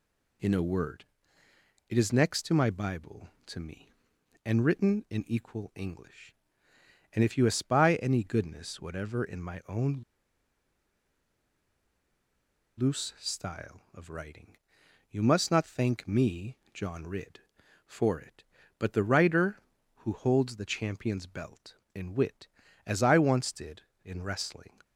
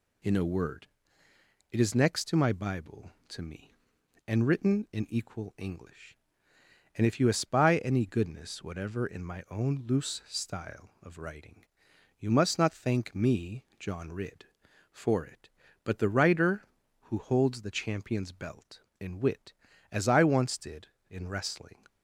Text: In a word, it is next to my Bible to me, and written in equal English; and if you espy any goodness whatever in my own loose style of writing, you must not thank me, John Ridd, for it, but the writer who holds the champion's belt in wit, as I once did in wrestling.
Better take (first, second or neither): second